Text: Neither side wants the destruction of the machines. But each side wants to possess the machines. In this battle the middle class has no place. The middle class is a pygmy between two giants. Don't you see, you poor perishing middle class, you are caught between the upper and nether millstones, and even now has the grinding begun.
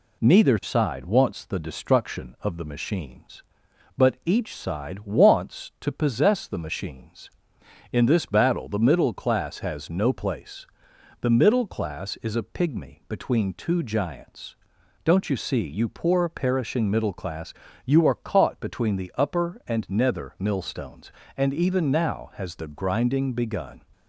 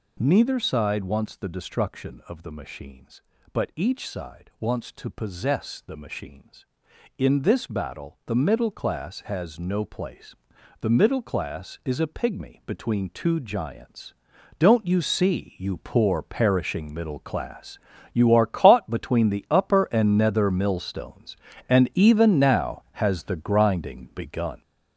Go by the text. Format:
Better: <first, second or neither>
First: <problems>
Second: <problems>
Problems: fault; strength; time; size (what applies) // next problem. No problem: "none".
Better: first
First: none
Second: gets louder; throughout; 7 dB